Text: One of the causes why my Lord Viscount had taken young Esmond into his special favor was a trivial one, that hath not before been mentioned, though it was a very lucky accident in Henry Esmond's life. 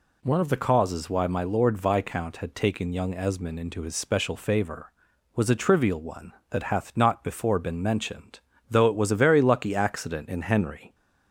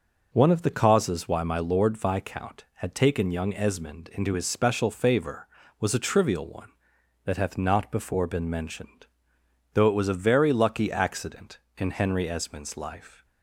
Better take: second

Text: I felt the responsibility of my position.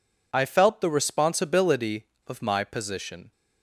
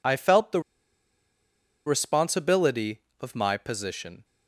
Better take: first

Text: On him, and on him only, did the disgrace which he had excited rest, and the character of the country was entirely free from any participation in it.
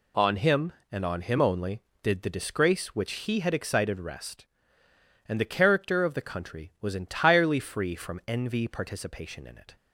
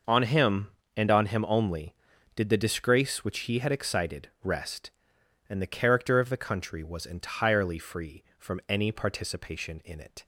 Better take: second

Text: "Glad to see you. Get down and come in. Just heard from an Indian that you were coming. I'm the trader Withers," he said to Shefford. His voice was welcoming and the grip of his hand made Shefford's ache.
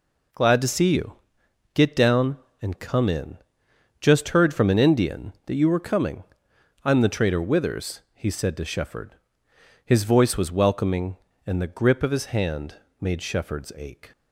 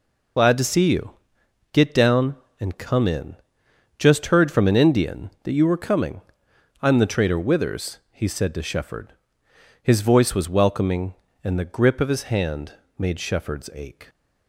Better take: first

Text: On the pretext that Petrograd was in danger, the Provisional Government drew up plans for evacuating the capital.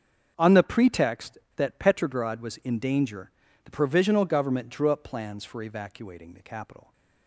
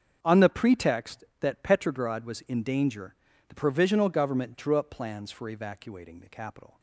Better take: neither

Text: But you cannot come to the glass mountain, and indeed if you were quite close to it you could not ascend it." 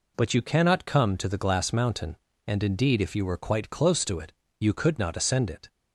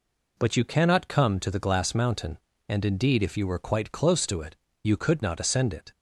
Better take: neither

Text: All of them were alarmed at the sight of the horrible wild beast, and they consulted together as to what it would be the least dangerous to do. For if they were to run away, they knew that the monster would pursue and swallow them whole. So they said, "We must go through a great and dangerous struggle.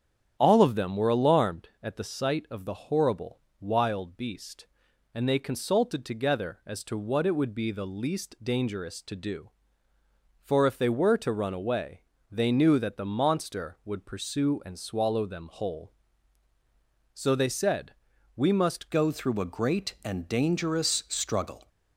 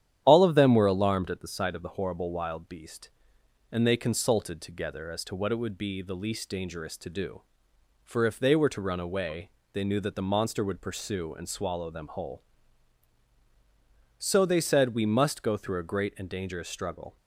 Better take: second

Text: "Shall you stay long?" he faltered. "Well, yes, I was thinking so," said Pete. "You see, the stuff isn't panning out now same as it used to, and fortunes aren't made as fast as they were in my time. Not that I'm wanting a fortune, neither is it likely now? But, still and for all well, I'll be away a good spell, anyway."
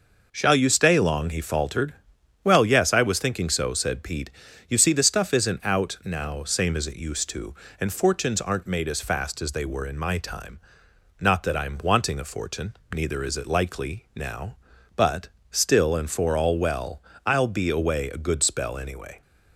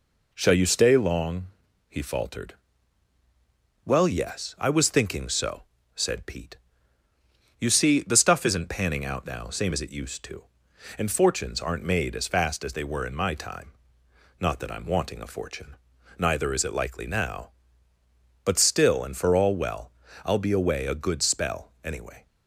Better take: second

